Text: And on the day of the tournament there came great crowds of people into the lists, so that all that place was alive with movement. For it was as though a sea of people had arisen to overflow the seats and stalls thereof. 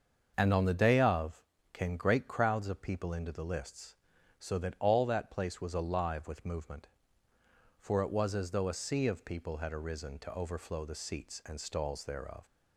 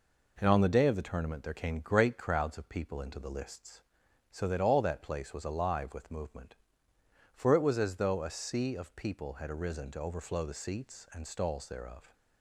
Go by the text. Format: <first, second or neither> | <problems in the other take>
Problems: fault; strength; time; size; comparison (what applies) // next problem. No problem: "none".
second | starts louder than the rest; until 1.3 s; 6.5 dB // skips "the tournament there"; at 1.5 s